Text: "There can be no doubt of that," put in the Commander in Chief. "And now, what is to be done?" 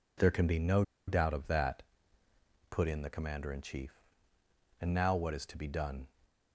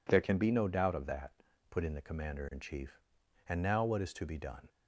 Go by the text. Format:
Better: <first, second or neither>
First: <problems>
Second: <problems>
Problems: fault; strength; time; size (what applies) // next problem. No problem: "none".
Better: second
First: pauses between "no" and "doubt"; slight; at 0.8 s; 0.25 s long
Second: none